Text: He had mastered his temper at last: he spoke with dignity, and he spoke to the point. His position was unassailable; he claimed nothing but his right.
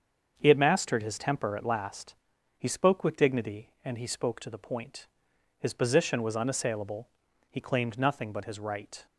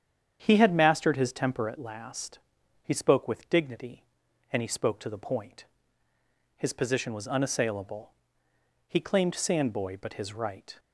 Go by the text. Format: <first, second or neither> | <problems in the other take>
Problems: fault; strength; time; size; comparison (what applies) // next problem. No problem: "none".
first | starts louder than the rest; strong; until 1.4 s; 8.5 dB; also in the first // says "sandboy" for "nothing"; at 9.3 s